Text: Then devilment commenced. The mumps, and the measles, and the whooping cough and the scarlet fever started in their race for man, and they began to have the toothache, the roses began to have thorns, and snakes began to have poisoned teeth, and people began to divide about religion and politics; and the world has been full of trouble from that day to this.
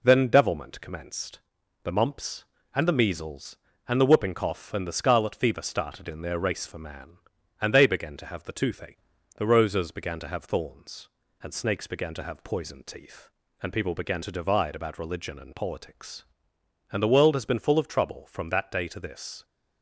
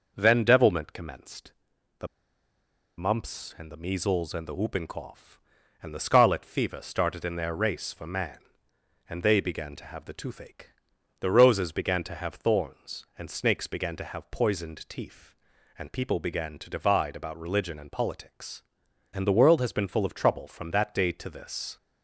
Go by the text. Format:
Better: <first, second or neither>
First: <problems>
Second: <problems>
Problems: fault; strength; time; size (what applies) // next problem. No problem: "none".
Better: first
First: none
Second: pauses between "The" and "mumps"; noticeable; at 2.0 s; 0.91 s long